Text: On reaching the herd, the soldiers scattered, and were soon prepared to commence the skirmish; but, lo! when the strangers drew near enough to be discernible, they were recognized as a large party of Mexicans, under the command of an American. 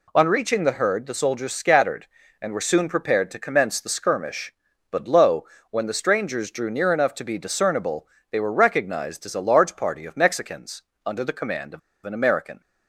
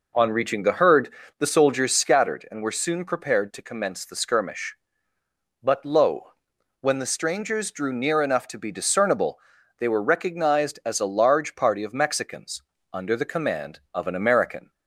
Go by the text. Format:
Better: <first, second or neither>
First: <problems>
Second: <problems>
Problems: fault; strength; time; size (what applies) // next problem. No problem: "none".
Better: second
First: pauses between "of" and "an"; slight; at 11.7 s; 0.26 s long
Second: none